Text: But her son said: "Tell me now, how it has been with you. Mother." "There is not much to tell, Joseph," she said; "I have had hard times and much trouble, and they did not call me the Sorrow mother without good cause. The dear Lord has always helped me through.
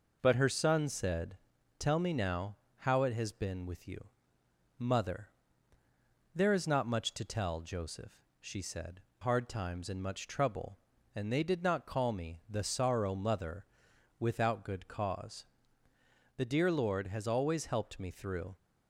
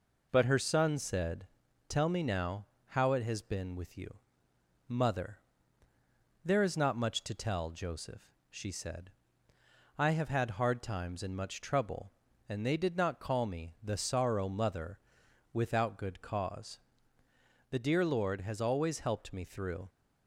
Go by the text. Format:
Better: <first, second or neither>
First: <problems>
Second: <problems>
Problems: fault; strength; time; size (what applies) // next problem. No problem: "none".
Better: second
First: skips "I have had"; at 9.1 s // pauses between "mother" and "without"; noticeable; at 13.6 s; 0.56 s long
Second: pauses between "mother" and "without"; noticeable; at 14.9 s; 0.56 s long